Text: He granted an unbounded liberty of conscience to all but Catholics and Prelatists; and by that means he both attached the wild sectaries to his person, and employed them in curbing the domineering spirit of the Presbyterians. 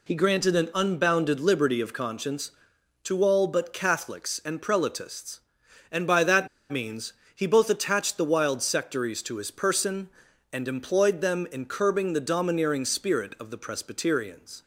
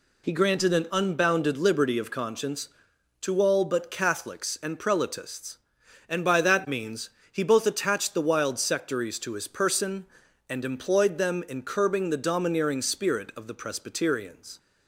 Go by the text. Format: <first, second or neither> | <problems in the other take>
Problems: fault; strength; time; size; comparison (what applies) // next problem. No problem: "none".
second | pauses between "that" and "means"; slight; at 6.4 s; 0.23 s long // pauses between "means" and "he"; slight; at 7.1 s; 0.22 s long; slight in the second